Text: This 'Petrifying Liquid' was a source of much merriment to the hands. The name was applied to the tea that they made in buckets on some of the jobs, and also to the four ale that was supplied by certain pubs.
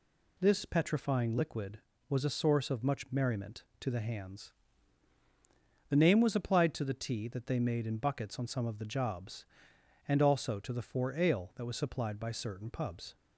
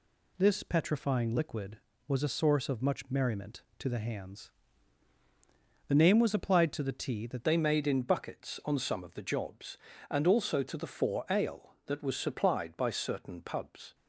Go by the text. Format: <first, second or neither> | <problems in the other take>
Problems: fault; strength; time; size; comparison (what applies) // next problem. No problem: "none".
first | changes voice at "they"; from 7.4 s on; 6.5 s long